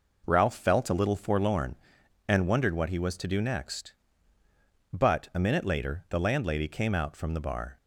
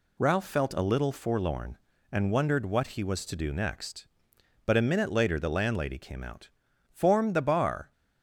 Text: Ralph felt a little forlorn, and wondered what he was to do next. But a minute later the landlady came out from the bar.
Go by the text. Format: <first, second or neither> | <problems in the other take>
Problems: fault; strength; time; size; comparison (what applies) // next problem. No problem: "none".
first | says "form" for "from"; at 6.8 s